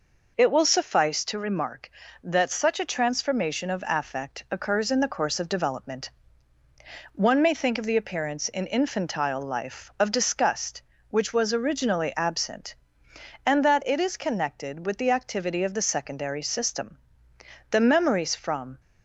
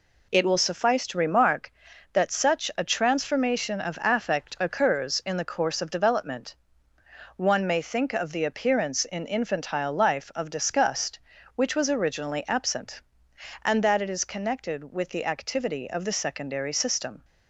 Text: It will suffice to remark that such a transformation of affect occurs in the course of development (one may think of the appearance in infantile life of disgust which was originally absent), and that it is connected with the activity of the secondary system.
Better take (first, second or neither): second